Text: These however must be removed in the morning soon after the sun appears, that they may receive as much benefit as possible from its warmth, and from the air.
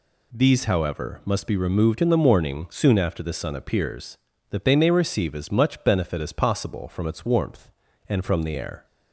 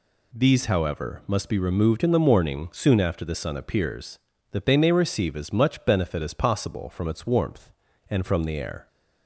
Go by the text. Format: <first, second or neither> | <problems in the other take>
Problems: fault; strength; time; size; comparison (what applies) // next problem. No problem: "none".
neither | none